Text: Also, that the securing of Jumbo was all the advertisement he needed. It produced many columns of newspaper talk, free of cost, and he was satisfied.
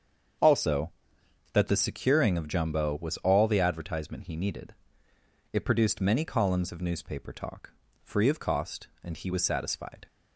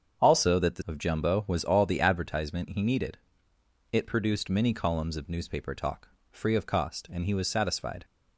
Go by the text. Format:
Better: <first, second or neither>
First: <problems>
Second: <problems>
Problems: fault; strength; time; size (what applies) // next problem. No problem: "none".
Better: first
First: starts louder than the rest; until 2.0 s; 7 dB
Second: starts louder than the rest; strong; until 1.2 s; 7.5 dB // skips "securing"; at 0.8 s